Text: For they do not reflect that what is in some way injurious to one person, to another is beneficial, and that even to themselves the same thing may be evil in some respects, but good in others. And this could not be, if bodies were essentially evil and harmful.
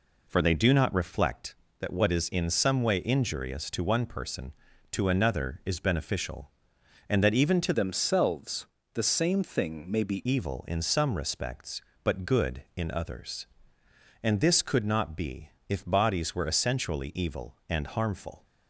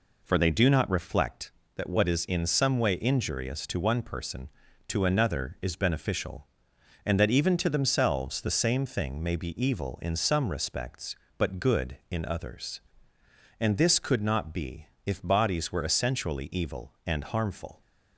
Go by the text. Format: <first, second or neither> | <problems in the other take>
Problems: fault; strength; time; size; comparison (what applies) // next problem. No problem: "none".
second | changes voice from "themselves" to "be"; from 7.7 to 10.2 s; 2.5 s long // pauses between "themselves" and "the"; slight; at 8.6 s; 0.26 s long